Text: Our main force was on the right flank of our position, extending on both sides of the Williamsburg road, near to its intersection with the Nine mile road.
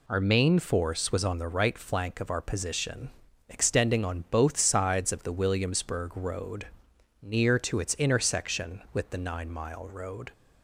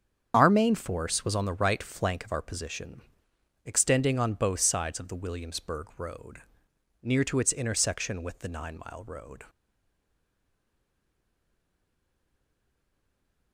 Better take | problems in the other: first | starts louder than the rest; strong; until 1.3 s; 7.5 dB // stays silent after the last word; strong; from 9.4 s on; 4.1 s long

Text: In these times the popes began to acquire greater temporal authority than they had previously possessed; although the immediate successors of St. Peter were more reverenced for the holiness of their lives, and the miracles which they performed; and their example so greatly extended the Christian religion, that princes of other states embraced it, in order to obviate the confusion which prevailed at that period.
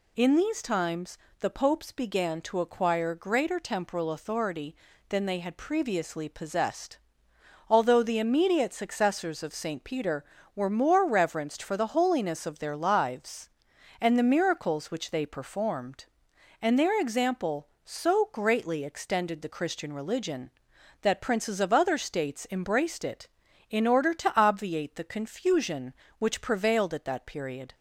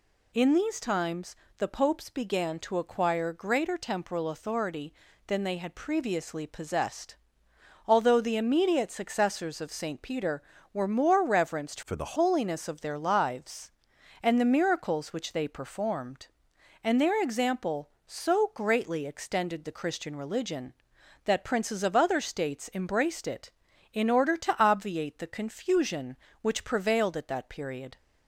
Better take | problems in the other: first | pauses between "times" and "the"; slight; at 1.3 s; 0.22 s long; slight in the first // changes voice from "for" to "the"; from 11.8 to 12.1 s; 0.3 s long

